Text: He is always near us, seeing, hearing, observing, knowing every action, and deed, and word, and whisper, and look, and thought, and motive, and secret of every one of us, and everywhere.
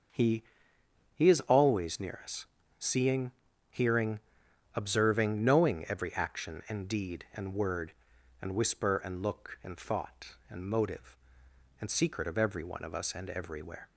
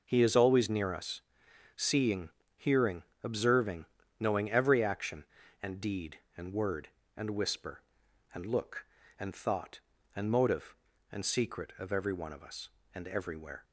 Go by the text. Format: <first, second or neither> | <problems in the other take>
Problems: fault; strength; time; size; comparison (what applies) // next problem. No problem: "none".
second | starts louder than the rest; until 1.8 s; 6.5 dB // says "He" twice; at 1.1 s